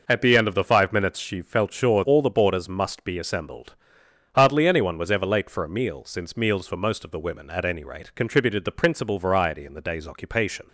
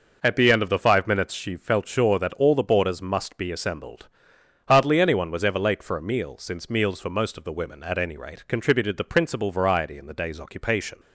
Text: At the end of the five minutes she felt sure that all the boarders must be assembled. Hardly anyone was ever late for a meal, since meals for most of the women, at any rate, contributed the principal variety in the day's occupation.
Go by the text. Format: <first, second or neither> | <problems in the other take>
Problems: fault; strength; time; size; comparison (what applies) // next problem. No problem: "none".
second | skips "that"; at 2.0 s